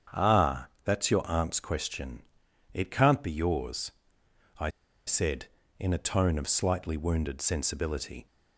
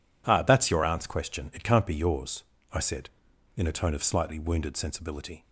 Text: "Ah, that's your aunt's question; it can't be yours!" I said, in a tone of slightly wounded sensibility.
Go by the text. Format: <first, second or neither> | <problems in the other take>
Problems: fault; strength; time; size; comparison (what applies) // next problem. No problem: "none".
second | starts louder than the rest; strong; until 1.3 s; 7.5 dB // pauses between "I" and "said"; at 4.7 s; 0.36 s long